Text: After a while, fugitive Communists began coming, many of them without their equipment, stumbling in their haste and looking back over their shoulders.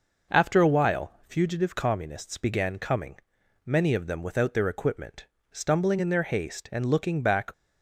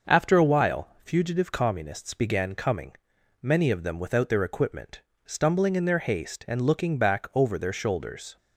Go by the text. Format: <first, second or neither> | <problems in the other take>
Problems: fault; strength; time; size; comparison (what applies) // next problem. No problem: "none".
second | stops before "over their shoulders"; at 7.5 s